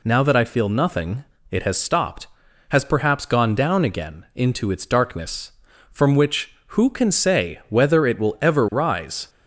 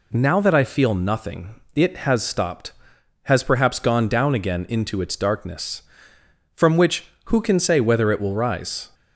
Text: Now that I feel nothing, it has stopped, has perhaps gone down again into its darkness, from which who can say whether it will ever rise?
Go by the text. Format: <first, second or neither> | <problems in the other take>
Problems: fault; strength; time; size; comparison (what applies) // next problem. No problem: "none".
first | skips "ever"; at 8.3 s